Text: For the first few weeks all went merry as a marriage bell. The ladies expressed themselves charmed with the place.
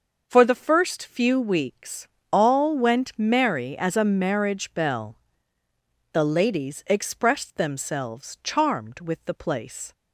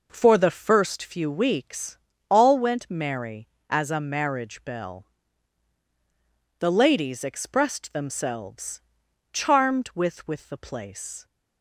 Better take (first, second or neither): first